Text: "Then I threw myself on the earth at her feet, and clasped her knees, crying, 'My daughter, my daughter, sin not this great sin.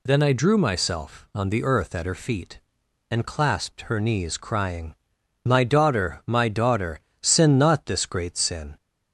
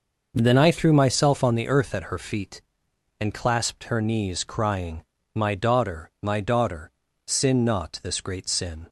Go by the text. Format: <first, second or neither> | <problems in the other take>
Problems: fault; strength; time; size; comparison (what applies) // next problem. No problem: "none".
second | says "drew" for "threw"; at 0.3 s